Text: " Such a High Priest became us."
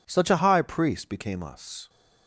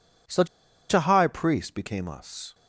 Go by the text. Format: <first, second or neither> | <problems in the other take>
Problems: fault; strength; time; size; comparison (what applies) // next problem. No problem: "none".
first | pauses between "Such" and "a"; at 0.4 s; 0.44 s long